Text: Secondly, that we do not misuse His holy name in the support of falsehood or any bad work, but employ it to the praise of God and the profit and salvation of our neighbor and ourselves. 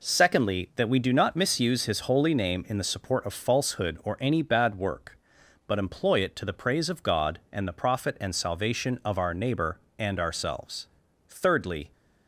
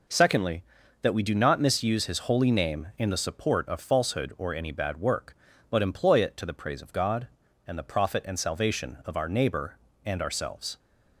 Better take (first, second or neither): second